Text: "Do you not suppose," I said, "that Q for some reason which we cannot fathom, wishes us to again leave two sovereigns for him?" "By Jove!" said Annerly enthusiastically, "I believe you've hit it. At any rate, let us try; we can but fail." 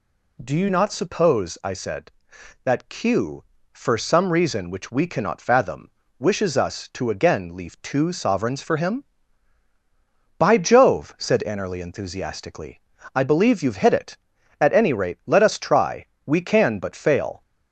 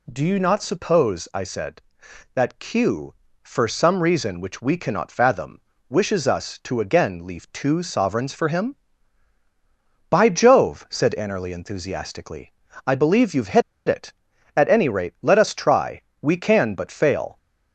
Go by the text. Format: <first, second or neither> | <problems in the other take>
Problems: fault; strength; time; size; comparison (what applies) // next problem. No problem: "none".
first | pauses between "hit" and "it"; slight; at 13.6 s; 0.26 s long